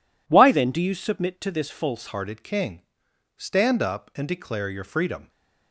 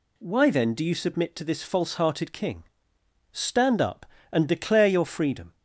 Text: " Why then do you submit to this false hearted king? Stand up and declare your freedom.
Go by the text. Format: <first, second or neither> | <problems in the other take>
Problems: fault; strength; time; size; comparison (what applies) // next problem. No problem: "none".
second | changes voice at "hearted"; from 2.0 s on; 3.2 s long